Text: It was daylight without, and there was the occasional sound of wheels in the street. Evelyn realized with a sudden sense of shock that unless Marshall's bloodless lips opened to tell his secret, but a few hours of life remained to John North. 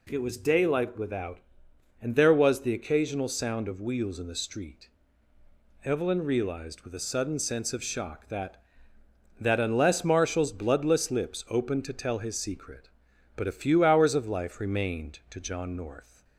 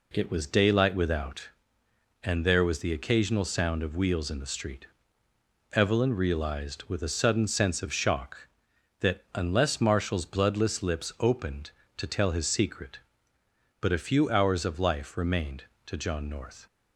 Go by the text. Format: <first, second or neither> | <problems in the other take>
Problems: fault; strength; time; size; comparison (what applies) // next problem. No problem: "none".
second | says "that" twice; at 9.3 s